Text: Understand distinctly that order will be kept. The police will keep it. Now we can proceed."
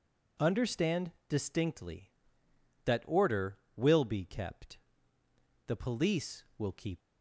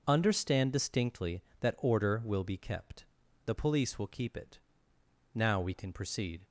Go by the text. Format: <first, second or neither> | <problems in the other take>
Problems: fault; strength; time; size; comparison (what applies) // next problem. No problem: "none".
second | pauses between "Understand" and "distinctly"; slight; at 1.1 s; 0.18 s long // stops before "it Now we can proceed"; at 7.0 s